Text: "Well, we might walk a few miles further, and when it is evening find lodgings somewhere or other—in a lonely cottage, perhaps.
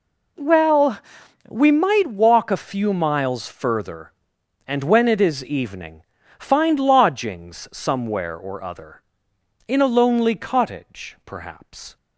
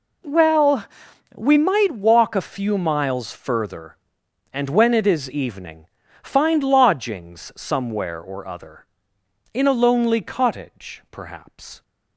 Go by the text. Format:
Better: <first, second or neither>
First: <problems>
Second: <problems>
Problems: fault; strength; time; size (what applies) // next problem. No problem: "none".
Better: neither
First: pauses between "evening" and "find"; at 6.0 s; 0.38 s long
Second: pauses between "evening" and "find"; at 5.8 s; 0.38 s long